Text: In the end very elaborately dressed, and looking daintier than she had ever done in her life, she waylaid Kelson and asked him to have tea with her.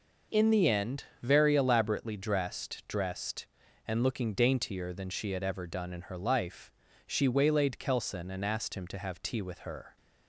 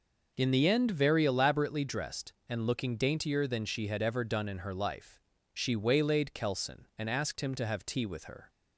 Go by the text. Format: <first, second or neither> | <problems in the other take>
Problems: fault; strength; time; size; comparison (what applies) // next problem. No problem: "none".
second | pauses between "end" and "very"; slight; at 1.0 s; 0.18 s long // says "dressed" twice; at 2.8 s